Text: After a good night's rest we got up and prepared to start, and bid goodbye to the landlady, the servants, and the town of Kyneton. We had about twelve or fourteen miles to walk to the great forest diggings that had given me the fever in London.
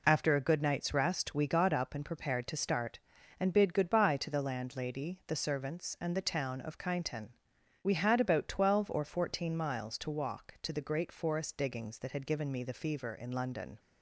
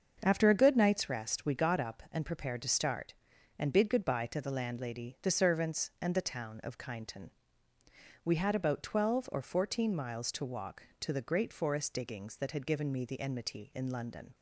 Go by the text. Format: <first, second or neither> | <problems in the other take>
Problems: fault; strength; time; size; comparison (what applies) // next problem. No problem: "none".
first | starts louder than the rest; until 1.2 s; 6.5 dB // says "enmity" for "fever"; at 13.2 s